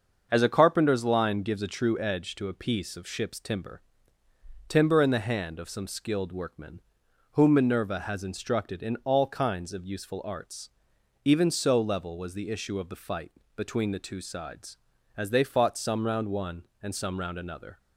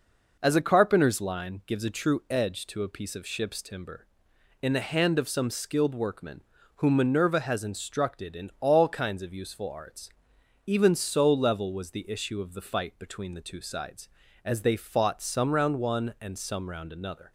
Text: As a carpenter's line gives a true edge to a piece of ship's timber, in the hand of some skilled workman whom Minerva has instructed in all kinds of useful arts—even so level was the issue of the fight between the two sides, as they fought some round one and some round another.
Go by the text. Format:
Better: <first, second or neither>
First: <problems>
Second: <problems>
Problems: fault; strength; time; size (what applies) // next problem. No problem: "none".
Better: second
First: starts louder than the rest; until 1.3 s; 6.5 dB // says "timber" twice; at 4.6 s // pauses between "workman" and "whom"; noticeable; at 6.8 s; 0.50 s long // pauses between "fight" and "between"; slight; at 13.3 s; 0.24 s long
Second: pauses between "workman" and "whom"; slight; at 6.4 s; 0.34 s long